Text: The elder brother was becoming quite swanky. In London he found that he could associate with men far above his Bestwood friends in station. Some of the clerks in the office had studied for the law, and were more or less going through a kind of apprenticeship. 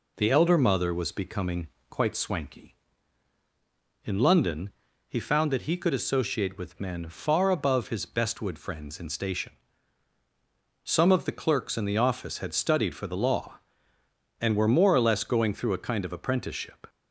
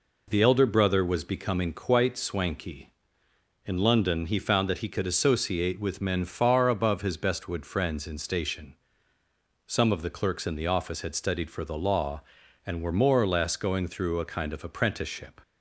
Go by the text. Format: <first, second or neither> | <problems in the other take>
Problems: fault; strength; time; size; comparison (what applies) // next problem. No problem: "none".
second | says "mother" for "brother"; at 0.5 s // pauses between "becoming" and "quite"; slight; at 1.6 s; 0.22 s long // pauses between "London" and "he"; slight; at 4.7 s; 0.36 s long